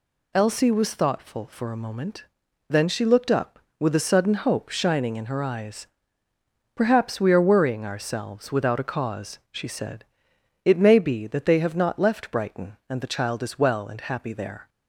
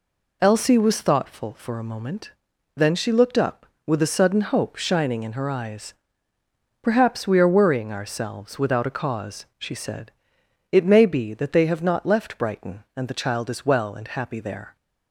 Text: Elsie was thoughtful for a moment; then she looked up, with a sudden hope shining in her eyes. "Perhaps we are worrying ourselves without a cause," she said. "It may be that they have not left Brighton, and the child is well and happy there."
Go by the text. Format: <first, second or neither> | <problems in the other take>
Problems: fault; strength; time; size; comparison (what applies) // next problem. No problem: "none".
first | starts louder than the rest; until 1.5 s; 3.5 dB